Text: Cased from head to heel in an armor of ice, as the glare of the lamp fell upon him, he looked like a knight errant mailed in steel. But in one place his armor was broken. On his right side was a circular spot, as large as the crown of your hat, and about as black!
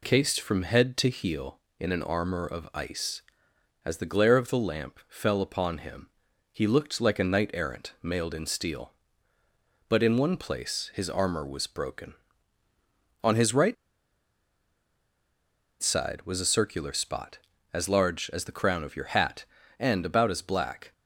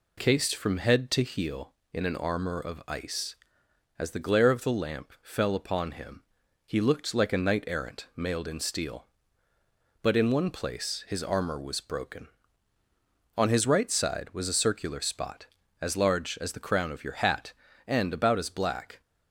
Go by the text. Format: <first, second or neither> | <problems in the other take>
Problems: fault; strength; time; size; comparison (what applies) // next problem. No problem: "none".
second | pauses between "right" and "side"; strong; at 13.7 s; 2.0 s long